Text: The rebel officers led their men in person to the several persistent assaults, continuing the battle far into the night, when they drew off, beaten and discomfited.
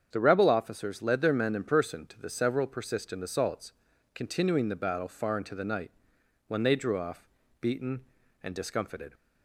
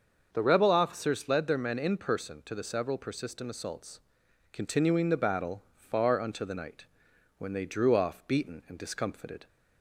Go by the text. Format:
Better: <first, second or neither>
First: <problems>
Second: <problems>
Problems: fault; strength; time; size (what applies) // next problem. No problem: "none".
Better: first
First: starts louder than the rest; strong; until 1.1 s; 8 dB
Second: starts louder than the rest; until 1.3 s; 6.5 dB // says "unto" for "into"; at 6.2 s